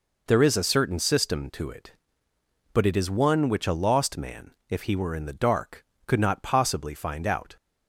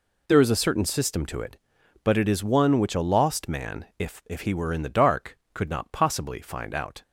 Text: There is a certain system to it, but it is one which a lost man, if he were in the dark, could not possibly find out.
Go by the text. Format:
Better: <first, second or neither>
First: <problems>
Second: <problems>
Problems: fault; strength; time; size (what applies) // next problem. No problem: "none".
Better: first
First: none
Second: says "if" twice; at 4.2 s